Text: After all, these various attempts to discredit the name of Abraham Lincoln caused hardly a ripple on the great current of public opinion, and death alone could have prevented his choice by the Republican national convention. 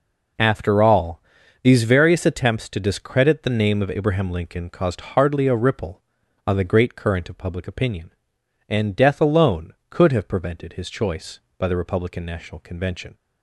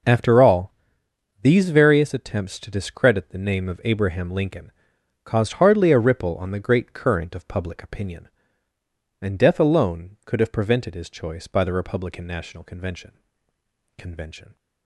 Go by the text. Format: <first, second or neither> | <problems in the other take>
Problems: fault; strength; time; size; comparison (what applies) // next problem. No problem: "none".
first | pauses between "Lincoln" and "caused"; noticeable; at 4.7 s; 0.52 s long // says "convention" twice; at 13.9 s